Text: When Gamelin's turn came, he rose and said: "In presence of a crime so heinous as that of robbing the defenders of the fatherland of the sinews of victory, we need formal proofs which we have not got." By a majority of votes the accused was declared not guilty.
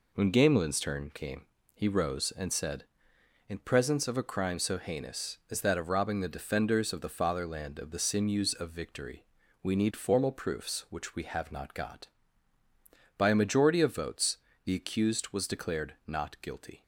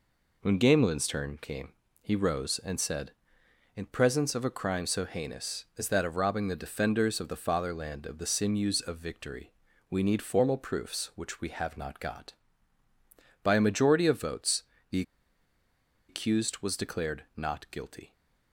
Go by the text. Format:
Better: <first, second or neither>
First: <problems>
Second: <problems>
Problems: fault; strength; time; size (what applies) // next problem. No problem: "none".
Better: first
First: pauses between "votes" and "the"; slight; at 14.3 s; 0.26 s long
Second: pauses between "votes" and "the"; slight; at 14.6 s; 0.26 s long // pauses between "the" and "accused"; at 15.0 s; 1.0 s long